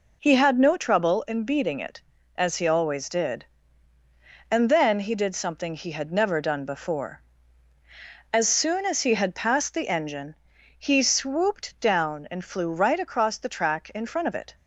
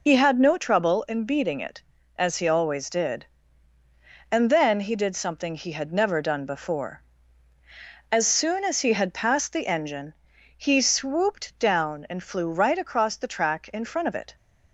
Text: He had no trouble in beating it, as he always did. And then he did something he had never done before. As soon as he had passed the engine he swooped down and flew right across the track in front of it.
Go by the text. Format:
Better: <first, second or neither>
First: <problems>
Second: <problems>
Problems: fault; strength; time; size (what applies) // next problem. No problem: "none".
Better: first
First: pauses between "engine" and "he"; at 10.3 s; 0.42 s long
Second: loses the start of "He"; at 0.0 s; 40 ms // pauses between "engine" and "he"; at 10.1 s; 0.42 s long